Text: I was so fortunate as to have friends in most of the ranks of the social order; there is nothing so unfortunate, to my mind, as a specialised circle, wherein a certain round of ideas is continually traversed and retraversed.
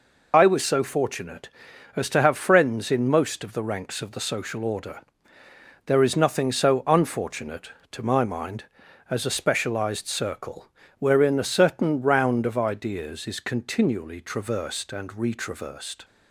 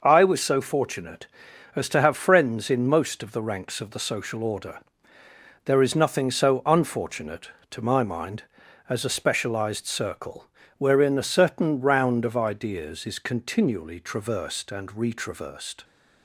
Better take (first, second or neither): second